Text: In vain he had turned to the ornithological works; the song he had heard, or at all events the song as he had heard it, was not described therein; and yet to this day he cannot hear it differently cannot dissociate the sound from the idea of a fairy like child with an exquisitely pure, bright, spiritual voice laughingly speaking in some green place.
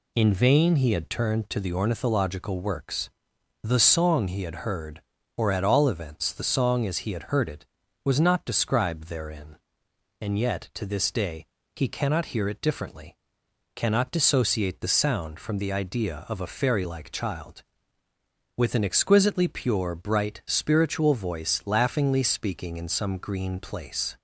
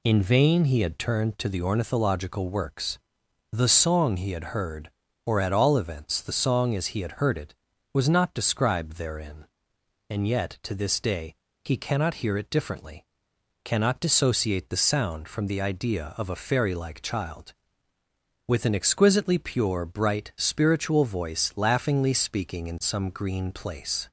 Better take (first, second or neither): neither